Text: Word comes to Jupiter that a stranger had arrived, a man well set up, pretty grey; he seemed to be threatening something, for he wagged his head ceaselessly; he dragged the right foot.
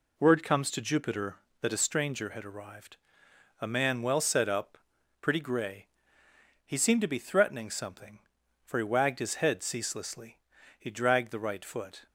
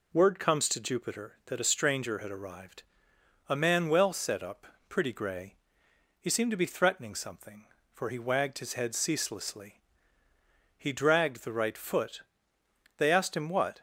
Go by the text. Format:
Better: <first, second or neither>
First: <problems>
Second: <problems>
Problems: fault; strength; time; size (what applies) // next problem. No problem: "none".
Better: first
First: none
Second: goes on to say "They asked him what"; noticeable; from 12.9 s on; 0.82 s long